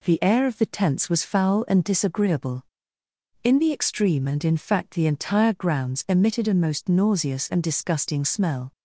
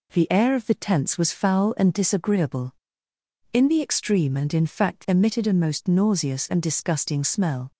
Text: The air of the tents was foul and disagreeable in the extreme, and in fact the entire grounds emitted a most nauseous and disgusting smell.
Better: first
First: none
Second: skips "the entire grounds"; at 5.0 s

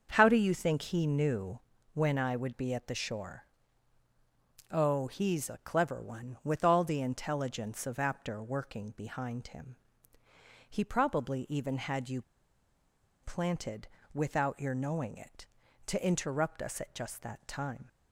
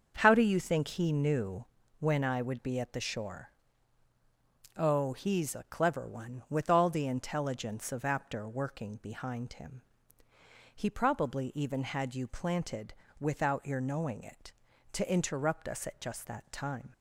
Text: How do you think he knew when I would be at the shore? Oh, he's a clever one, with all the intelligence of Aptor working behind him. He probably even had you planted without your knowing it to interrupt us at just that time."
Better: second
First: starts louder than the rest; until 1.1 s; 6.5 dB // pauses between "knew" and "when"; slight; at 1.5 s; 0.34 s long // pauses between "you" and "planted"; at 12.2 s; 1.0 s long // pauses between "planted" and "without"; slight; at 13.8 s; 0.26 s long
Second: starts louder than the rest; until 1.2 s; 6.5 dB // pauses between "knew" and "when"; slight; at 1.6 s; 0.34 s long // pauses between "planted" and "without"; slight; at 12.9 s; 0.26 s long

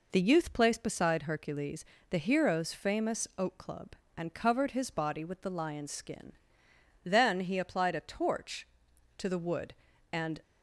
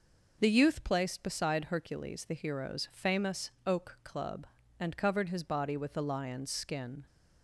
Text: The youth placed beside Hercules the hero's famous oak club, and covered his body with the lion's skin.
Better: second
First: pauses between "Hercules" and "the"; slight; at 1.8 s; 0.24 s long // goes on to say "Then he applied a torch to the wood and"; strong; from 7.0 s on; 3.3 s long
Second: none

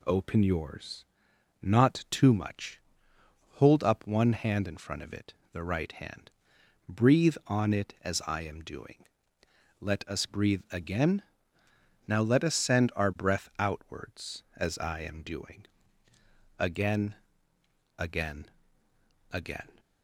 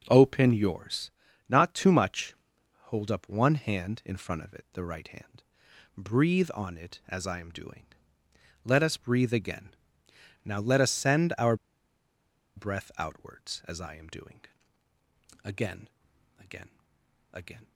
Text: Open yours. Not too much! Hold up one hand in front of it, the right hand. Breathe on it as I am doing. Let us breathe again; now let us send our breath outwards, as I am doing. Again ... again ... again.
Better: first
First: none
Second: pauses between "our" and "breath"; at 11.5 s; 1.0 s long

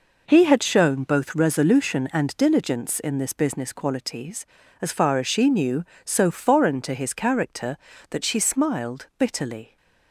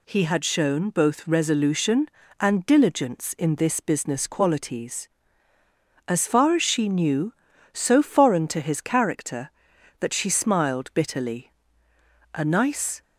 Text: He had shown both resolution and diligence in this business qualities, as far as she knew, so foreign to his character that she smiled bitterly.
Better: first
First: none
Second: goes on to say "A nice"; noticeable; from 12.3 s on; 0.66 s long

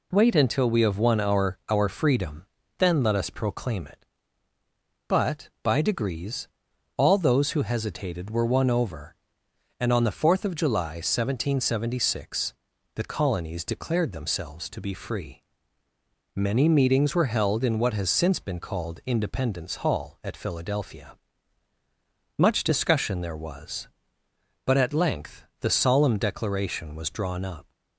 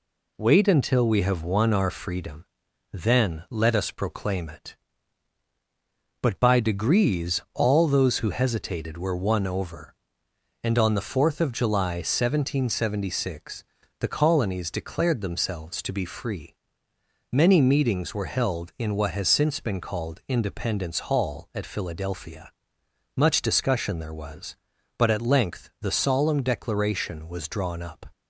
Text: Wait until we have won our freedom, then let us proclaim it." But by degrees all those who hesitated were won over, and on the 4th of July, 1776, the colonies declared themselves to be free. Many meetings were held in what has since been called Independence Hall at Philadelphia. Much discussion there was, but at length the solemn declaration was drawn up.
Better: second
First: says "our" twice; at 1.6 s // pauses between "degrees" and "all"; noticeable; at 6.4 s; 0.48 s long // pauses between "length" and "the"; slight; at 25.4 s; 0.16 s long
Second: none

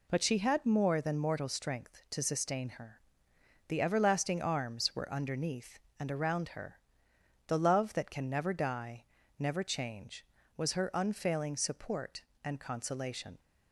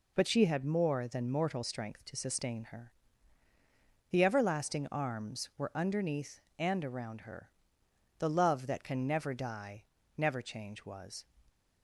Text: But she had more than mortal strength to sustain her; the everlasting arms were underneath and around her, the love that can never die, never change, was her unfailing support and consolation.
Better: first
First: none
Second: stops before "her unfailing support and consolation"; at 11.4 s

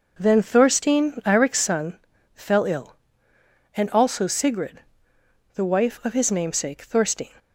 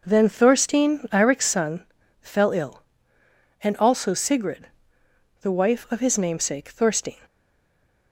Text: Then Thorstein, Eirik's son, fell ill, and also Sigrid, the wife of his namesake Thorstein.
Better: first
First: none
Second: stays silent after the last word; slight; from 7.2 s on; 0.9 s long

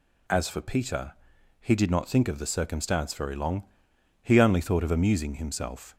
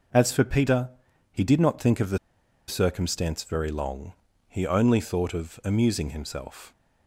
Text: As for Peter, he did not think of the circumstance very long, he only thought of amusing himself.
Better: first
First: none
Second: pauses between "the" and "circumstance"; noticeable; at 2.1 s; 0.50 s long

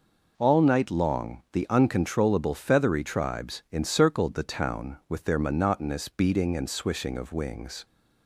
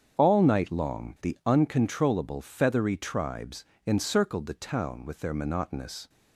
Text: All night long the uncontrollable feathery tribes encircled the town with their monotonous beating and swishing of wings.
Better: first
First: none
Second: starts louder than the rest; strong; until 1.2 s; 7.5 dB // pauses between "tribes" and "encircled"; slight; at 3.6 s; 0.22 s long // stops before "beating and swishing of wings"; at 6.0 s

